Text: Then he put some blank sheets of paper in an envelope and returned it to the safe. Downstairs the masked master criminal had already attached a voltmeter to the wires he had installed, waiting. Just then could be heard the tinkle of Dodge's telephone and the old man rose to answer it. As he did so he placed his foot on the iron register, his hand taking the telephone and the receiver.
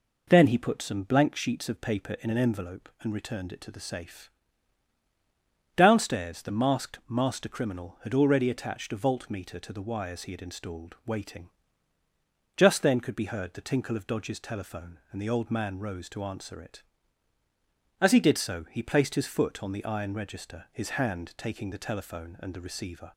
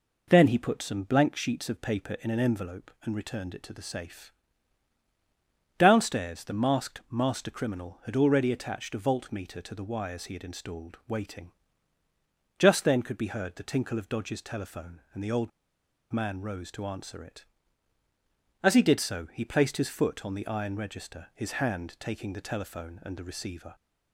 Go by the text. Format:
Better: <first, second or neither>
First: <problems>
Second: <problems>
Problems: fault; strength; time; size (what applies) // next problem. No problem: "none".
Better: first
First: none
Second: pauses between "old" and "man"; noticeable; at 15.5 s; 0.62 s long